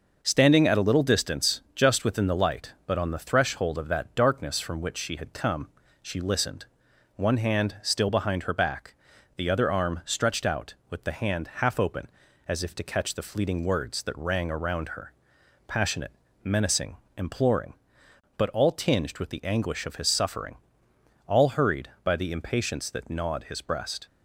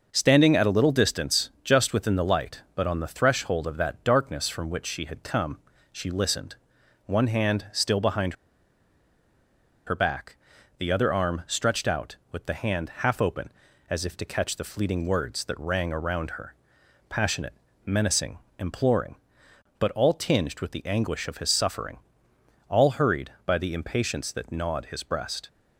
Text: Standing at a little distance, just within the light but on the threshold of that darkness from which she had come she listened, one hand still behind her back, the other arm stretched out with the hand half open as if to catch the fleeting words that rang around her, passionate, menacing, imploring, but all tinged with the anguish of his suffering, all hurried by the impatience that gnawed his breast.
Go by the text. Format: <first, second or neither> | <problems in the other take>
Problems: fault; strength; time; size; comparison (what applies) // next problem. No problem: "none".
first | pauses between "come" and "she"; slight; at 5.5 s; 0.34 s long; slight in the first // pauses between "behind" and "her"; strong; at 8.3 s; 1.5 s long